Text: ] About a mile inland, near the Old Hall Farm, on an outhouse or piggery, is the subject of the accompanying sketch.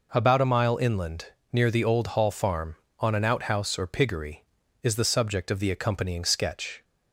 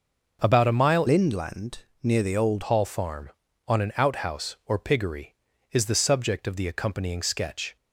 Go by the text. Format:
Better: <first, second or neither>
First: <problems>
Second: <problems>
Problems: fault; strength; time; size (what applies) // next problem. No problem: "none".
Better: first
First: none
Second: starts louder than the rest; until 1.4 s; 6 dB // changes voice from "inland" to "Old"; from 1.0 to 2.6 s; 1.6 s long